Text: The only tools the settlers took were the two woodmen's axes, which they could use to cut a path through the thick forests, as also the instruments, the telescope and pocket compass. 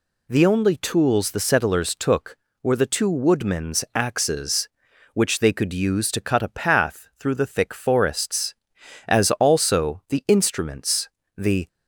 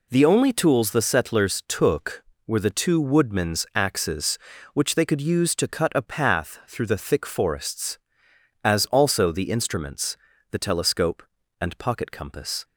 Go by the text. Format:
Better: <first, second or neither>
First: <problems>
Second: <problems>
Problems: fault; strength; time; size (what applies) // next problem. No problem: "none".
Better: second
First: stops before "telescope and pocket compass"; at 11.6 s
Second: none